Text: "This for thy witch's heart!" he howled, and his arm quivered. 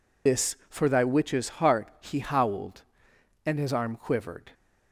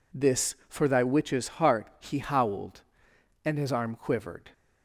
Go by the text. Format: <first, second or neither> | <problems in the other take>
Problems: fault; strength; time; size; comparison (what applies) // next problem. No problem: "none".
second | loses the start of "This"; at 0.2 s; 110 ms